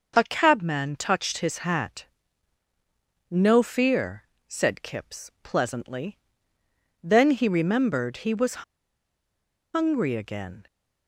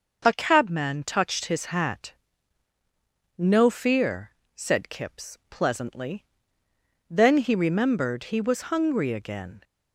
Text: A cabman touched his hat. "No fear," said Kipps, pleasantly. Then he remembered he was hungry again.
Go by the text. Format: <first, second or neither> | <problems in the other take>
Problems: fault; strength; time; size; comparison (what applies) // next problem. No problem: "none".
second | pauses between "was" and "hungry"; at 8.6 s; 1.1 s long